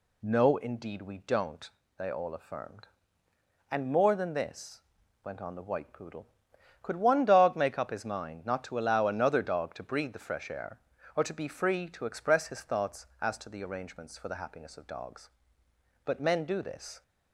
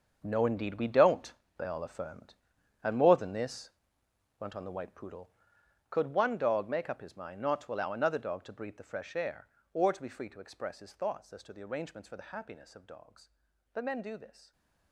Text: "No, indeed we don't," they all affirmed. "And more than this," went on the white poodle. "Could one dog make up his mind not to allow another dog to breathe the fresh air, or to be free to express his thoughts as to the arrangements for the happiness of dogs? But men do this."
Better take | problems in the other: first | gets quieter; strong; throughout; 13 dB // stays silent after the last word; slight; from 14.4 s on; 0.5 s long

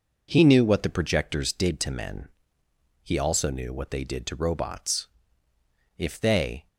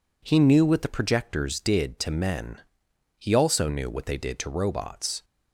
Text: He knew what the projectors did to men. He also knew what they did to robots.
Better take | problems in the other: second | goes on to say "If they"; noticeable; from 5.9 s on; 0.70 s long

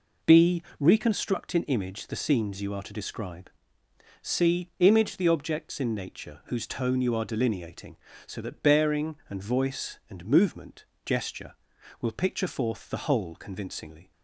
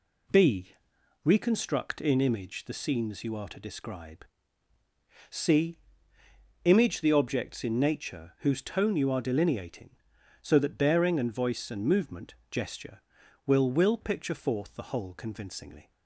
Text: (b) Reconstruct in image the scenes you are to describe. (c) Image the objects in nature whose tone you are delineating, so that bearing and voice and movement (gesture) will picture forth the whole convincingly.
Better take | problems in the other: first | says "will" twice; at 13.7 s

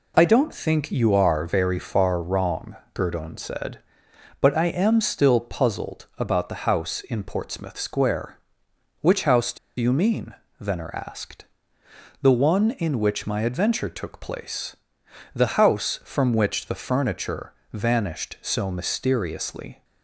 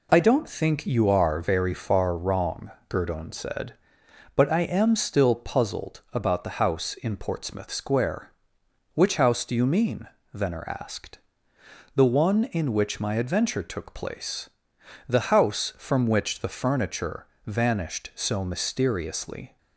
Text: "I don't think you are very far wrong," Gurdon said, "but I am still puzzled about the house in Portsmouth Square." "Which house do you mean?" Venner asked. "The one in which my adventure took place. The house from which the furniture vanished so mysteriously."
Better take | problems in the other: second | pauses between "do" and "you"; slight; at 9.5 s; 0.21 s long // pauses between "furniture" and "vanished"; slight; at 17.5 s; 0.20 s long; slight in the second

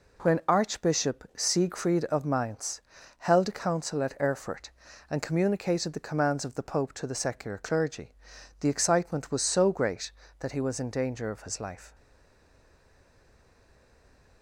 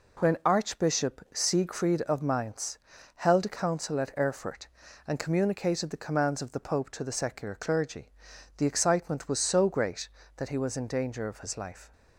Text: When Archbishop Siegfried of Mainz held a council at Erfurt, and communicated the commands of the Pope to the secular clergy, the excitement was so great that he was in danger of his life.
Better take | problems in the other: second | pauses between "Mainz" and "held"; slight; at 2.8 s; 0.34 s long; slight in the second // stays silent after the last word; from 11.9 s on; 2.5 s long

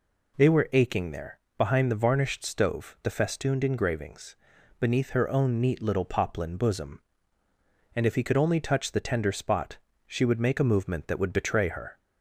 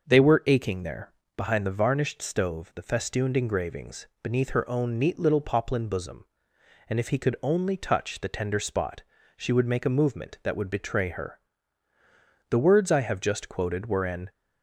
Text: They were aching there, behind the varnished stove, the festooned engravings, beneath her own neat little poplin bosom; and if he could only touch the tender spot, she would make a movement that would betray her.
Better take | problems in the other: first | starts louder than the rest; until 1.1 s; 6 dB // goes on to say "The words I have just quoted were an"; strong; from 12.5 s on; 1.8 s long

